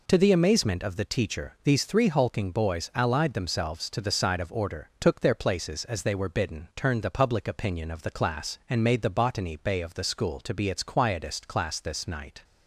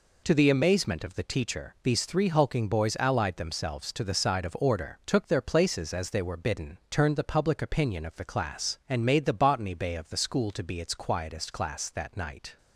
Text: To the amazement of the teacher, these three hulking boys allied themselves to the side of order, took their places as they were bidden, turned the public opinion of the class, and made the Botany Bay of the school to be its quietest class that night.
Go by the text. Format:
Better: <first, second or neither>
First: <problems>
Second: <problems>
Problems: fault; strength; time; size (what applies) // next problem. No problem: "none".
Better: second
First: says "this" for "that"; at 11.7 s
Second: none